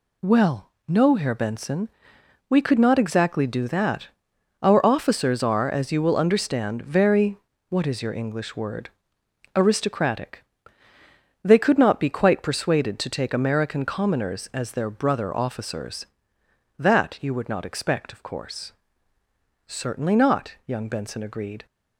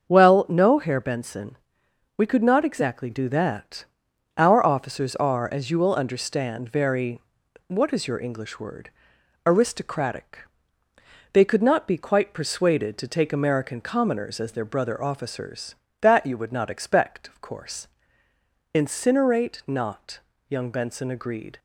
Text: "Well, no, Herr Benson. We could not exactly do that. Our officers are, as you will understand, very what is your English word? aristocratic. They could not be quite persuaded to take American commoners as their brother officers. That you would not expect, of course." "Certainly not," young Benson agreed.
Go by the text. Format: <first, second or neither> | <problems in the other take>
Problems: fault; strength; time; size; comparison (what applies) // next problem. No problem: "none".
first | starts louder than the rest; until 1.1 s; 7 dB // pauses between "very" and "what"; noticeable; at 7.2 s; 0.48 s long; slight in the first // says "Incinerate" for "Certainly"; at 18.7 s